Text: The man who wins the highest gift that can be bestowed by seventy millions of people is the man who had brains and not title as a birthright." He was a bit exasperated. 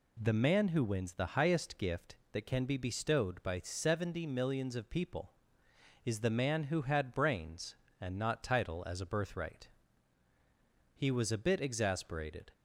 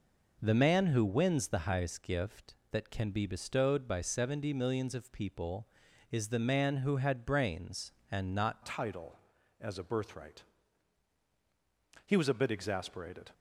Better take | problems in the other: first | changes voice at "title"; from 8.6 s on; 4.7 s long

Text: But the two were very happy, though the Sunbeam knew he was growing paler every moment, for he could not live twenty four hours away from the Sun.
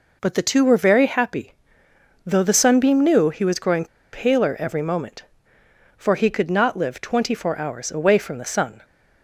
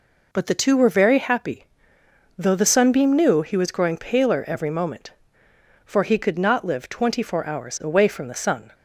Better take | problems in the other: second | pauses between "growing" and "paler"; slight; at 3.8 s; 0.26 s long

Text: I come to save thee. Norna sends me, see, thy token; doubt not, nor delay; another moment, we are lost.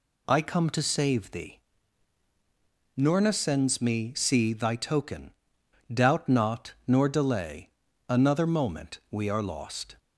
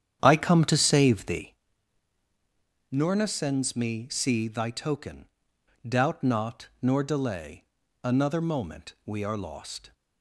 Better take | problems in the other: first | starts louder than the rest; strong; until 1.5 s; 9 dB

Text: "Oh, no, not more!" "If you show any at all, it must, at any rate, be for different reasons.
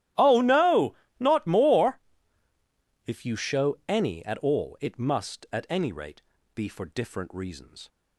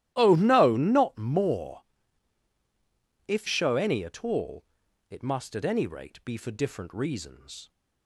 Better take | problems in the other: first | starts louder than the rest; strong; until 1.1 s; 13.5 dB; strong in the first // skips "you"; at 3.4 s

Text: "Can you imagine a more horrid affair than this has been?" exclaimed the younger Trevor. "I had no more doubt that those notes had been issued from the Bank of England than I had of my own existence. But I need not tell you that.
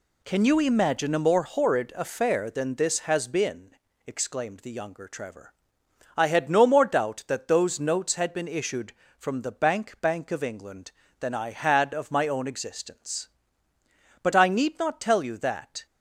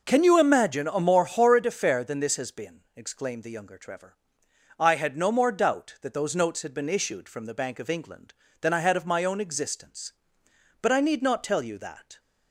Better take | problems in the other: second | says "Bank" twice; at 9.9 s

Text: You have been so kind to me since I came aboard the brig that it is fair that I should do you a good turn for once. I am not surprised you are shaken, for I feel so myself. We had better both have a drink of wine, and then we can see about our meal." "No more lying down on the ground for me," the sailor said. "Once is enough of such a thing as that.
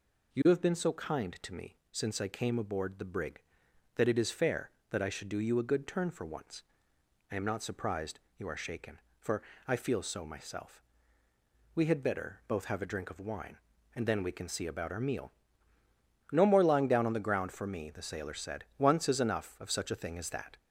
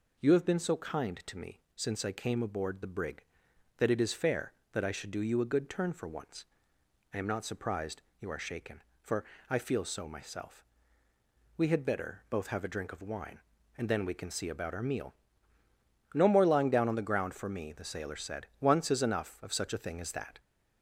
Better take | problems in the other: neither | pauses between "me" and "since"; slight; the same in both // pauses between "surprised" and "you"; slight; the same in both // pauses between "for" and "I"; slight; the same in both

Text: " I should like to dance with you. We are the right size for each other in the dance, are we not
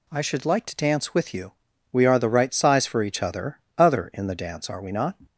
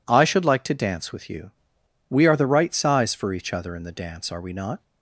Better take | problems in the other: second | says "other" twice; at 3.7 s

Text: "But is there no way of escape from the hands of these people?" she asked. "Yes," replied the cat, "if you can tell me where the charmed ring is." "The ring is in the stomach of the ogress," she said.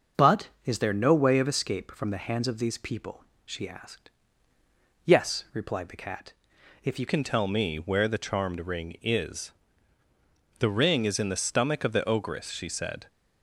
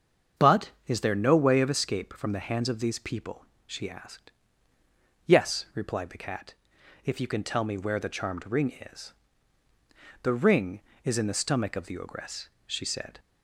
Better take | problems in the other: second | starts louder than the rest; until 1.3 s; 6.5 dB; strong in the second // changes voice at "can"; from 7.0 s on; 6.0 s long

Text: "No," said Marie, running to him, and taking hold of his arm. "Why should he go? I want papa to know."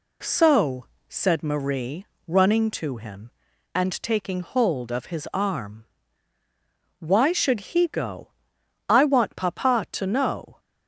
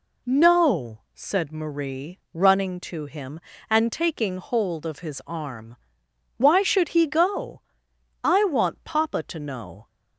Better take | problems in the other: second | says "So" for "No"; at 0.2 s

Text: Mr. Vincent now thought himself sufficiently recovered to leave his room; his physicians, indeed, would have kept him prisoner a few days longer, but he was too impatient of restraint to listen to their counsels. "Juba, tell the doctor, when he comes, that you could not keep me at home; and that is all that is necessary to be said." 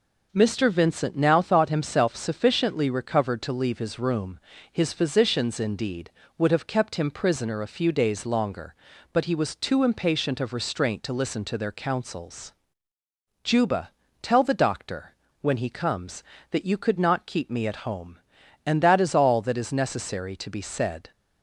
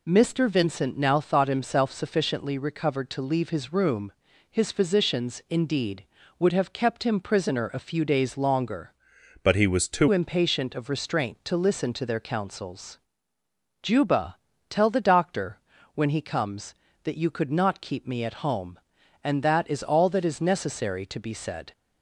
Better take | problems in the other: first | changes voice from "but" to "too"; from 9.4 to 10.0 s; 0.6 s long

